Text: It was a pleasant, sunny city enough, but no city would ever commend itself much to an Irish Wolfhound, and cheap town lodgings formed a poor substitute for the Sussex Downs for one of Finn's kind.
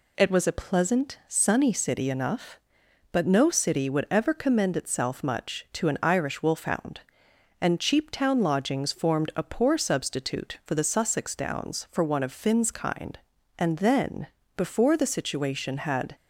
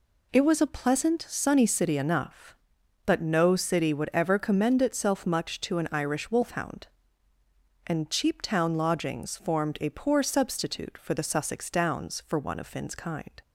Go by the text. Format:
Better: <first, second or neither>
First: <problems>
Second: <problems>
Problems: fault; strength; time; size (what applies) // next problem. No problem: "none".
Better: second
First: goes on to say "And then before the situation had"; strong; from 13.5 s on; 2.5 s long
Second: none